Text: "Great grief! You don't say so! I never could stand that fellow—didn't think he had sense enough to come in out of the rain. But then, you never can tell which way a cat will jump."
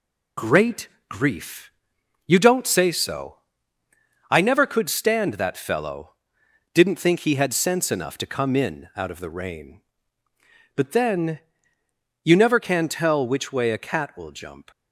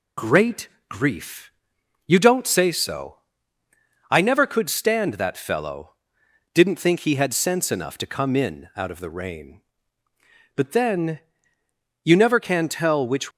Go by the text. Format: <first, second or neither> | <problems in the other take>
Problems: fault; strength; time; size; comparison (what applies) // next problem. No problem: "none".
first | pauses between "Great" and "grief"; slight; at 0.6 s; 0.22 s long; slight in the first // stops before "way a cat will jump"; at 13.3 s